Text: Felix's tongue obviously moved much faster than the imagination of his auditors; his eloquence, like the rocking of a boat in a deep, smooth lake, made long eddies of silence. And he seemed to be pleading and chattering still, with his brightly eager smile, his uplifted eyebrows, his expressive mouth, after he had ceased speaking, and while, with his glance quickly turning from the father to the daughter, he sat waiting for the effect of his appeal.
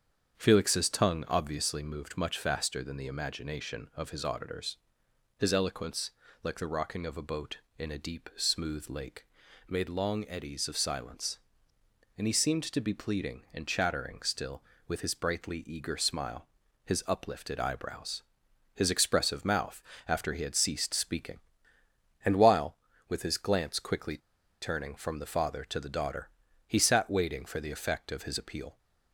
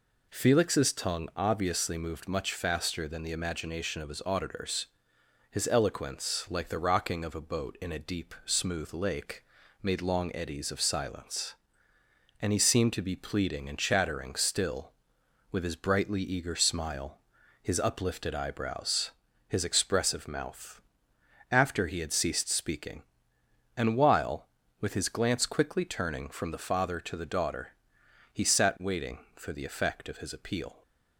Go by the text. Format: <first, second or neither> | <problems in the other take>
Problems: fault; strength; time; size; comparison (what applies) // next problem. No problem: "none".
second | starts louder than the rest; strong; until 1.3 s; 7.5 dB // pauses between "quickly" and "turning"; at 24.1 s; 0.43 s long